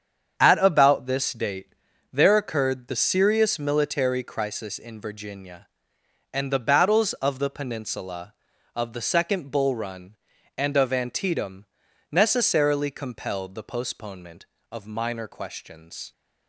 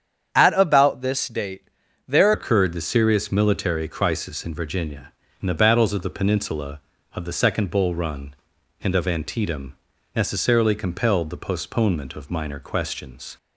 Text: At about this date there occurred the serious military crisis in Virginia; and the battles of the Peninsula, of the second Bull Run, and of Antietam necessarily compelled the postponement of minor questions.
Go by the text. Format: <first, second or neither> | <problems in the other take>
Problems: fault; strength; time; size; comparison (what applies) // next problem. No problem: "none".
first | starts louder than the rest; strong; until 1.3 s; 8.5 dB; strong in the first // pauses between "date" and "there"; at 1.6 s; 0.40 s long; also in the first // changes voice at "occurred"; from 2.3 s on; 11.0 s long // pauses between "Antietam" and "necessarily"; at 9.7 s; 0.40 s long; noticeable in the first